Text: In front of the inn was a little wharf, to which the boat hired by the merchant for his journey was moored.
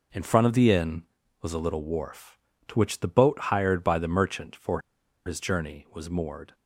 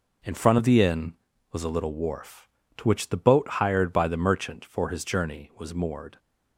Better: second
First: pauses between "for" and "his"; at 4.8 s; 0.45 s long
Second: none

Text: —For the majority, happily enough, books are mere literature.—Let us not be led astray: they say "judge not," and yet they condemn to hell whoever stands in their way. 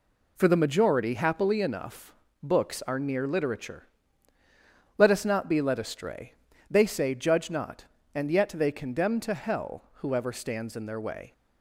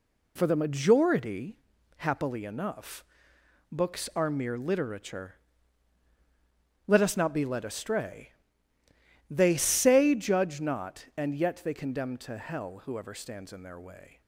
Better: second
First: says "near" for "mere"; at 2.9 s // pauses between "hell" and "whoever"; slight; at 9.8 s; 0.18 s long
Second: none

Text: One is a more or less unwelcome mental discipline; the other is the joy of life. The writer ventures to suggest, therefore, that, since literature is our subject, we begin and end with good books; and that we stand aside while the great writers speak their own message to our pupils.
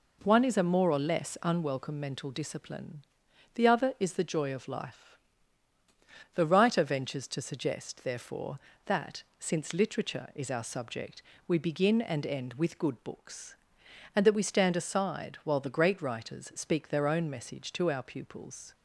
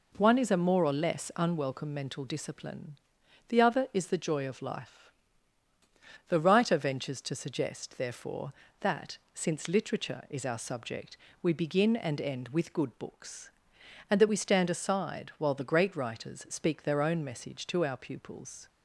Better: neither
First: none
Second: none

